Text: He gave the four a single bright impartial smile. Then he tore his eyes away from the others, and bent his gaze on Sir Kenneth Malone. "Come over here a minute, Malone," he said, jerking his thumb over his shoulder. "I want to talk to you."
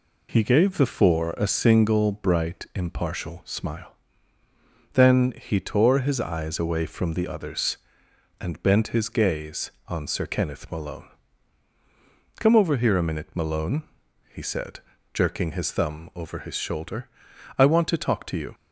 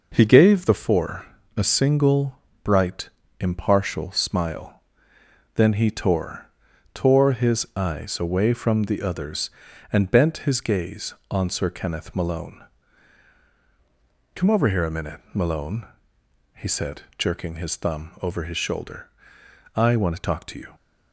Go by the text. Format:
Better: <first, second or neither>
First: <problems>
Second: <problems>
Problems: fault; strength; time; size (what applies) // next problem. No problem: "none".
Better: first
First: none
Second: pauses between "four" and "a"; slight; at 1.2 s; 0.32 s long // pauses between "single" and "bright"; slight; at 2.3 s; 0.26 s long // pauses between "bright" and "impartial"; slight; at 3.0 s; 0.32 s long // says "tore" twice; at 6.9 s